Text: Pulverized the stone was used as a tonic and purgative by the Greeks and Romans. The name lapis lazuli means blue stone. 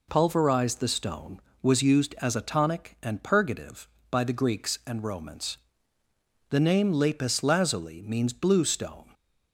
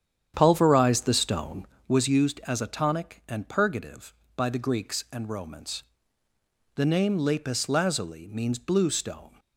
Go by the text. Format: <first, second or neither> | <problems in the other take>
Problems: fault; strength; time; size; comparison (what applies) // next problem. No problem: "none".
first | starts louder than the rest; strong; until 2.0 s; 9 dB